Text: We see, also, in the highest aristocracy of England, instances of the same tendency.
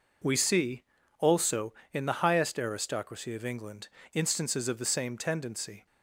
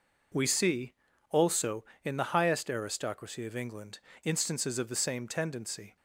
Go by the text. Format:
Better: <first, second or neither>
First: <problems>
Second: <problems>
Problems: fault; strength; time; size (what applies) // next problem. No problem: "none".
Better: neither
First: none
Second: none